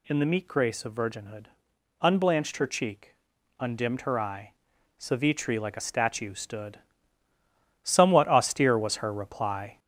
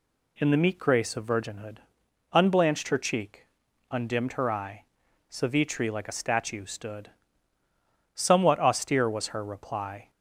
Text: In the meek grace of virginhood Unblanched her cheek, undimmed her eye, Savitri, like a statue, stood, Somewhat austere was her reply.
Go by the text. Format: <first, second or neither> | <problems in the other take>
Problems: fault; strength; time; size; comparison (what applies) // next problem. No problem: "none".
second | gets louder; noticeable; throughout; 4.5 dB // pauses between "virginhood" and "Unblanched"; noticeable; at 1.4 s; 0.56 s long; noticeable in the second